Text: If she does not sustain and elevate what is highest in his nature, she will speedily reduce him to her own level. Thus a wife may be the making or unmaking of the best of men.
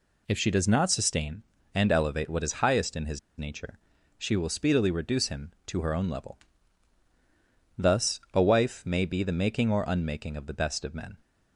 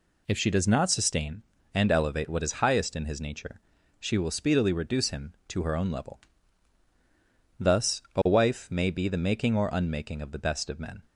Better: second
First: pauses between "his" and "nature"; slight; at 3.1 s; 0.19 s long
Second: none

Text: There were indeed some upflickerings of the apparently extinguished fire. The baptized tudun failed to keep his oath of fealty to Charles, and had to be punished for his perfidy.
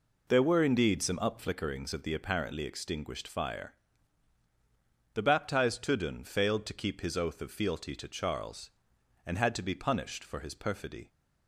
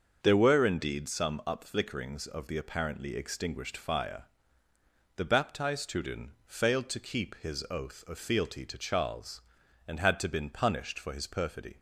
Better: first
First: none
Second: starts louder than the rest; until 1.2 s; 6.5 dB // says "been" for "be"; at 10.2 s

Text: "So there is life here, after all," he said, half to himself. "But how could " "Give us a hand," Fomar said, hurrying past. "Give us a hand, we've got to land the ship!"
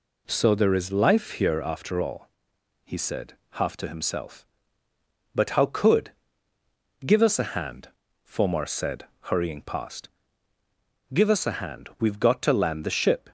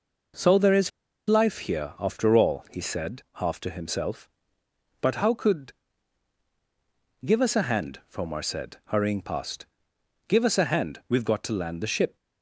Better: first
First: none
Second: pauses between "is" and "life"; at 0.9 s; 0.37 s long

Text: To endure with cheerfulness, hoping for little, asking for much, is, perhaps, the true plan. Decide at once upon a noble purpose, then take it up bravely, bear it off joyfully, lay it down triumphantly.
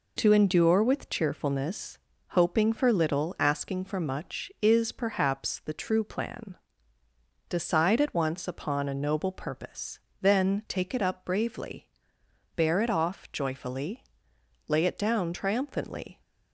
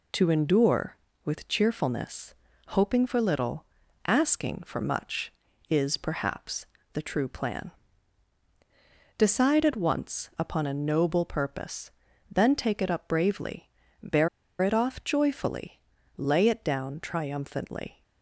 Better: first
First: none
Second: pauses between "bear" and "it"; slight; at 14.2 s; 0.33 s long

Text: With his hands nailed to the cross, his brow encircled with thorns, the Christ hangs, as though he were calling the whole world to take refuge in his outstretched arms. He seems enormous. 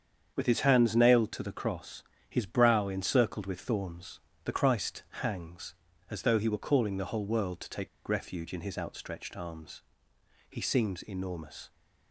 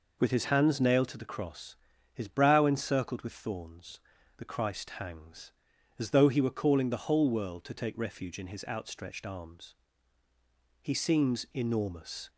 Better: second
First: starts louder than the rest; strong; until 1.3 s; 7.5 dB // pauses between "take" and "refuge"; slight; at 7.8 s; 0.18 s long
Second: none

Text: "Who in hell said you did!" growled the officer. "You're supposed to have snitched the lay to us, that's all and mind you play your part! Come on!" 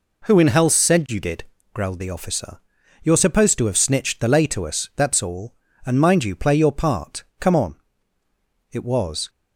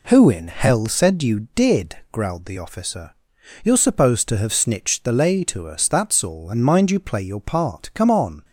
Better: second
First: goes on to say "It was"; from 8.7 s on; 0.58 s long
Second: none

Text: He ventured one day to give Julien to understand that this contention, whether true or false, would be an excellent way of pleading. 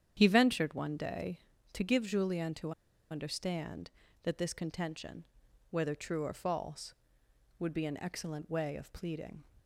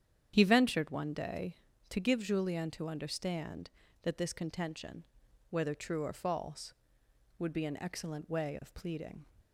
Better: second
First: starts louder than the rest; strong; until 1.1 s; 9 dB // pauses between "to" and "understand"; at 2.7 s; 0.38 s long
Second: starts louder than the rest; strong; until 1.3 s; 9 dB

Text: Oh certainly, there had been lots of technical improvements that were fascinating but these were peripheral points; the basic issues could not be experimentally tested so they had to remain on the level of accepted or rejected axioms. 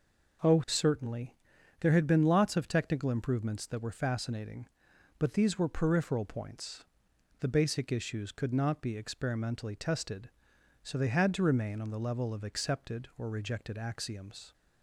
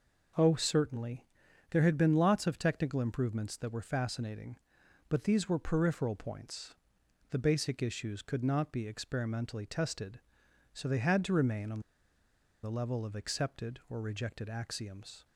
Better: first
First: none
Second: pauses between "on" and "the"; noticeable; at 11.8 s; 0.82 s long

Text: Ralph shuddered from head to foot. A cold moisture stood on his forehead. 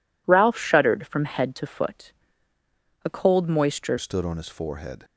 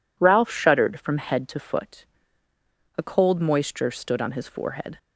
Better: second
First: changes voice at "stood"; from 3.9 s on; 1.1 s long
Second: none

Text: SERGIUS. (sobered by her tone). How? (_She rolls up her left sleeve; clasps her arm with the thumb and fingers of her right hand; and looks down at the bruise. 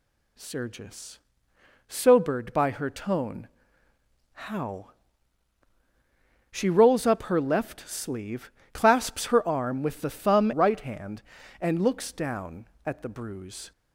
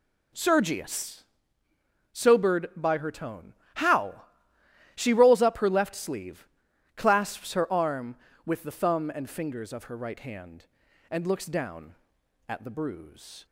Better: second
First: skips "and fingers of her"; at 10.5 s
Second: none

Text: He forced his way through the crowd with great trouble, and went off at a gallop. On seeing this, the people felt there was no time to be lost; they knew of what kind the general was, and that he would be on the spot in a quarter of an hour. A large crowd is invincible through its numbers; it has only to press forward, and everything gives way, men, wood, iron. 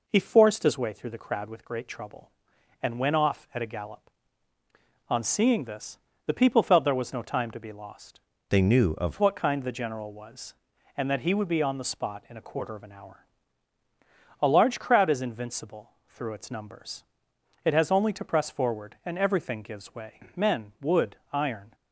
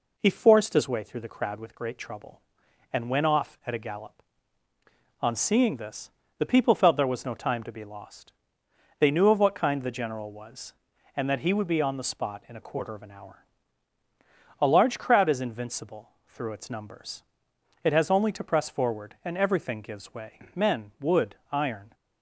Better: second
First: changes voice from "they" to "of"; from 8.4 to 9.1 s; 0.7 s long // pauses between "invincible" and "through"; slight; at 15.9 s; 0.18 s long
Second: pauses between "invincible" and "through"; slight; at 16.0 s; 0.18 s long

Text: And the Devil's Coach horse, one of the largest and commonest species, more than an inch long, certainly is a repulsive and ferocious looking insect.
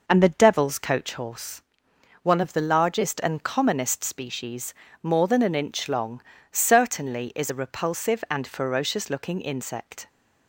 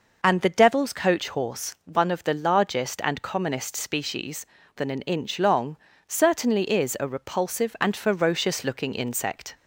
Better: first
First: none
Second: skips "more"; at 4.6 s

